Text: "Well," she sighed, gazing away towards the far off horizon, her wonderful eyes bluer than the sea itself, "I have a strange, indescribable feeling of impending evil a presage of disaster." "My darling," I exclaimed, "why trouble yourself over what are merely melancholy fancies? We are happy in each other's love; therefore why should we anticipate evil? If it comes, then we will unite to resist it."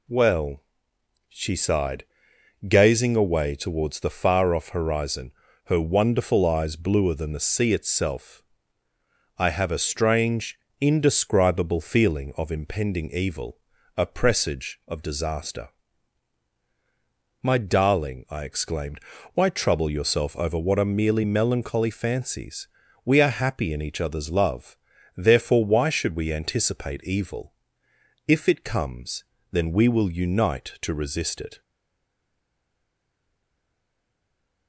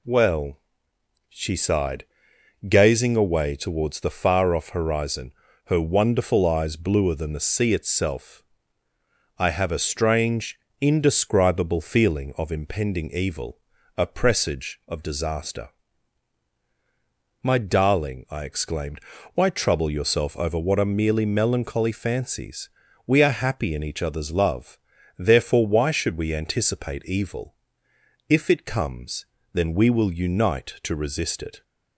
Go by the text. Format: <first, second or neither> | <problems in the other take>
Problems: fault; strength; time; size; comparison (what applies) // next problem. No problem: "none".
second | pauses between "evil" and "a"; at 13.5 s; 0.38 s long; also in the second // stays silent after the last word; strong; from 31.6 s on; 3.0 s long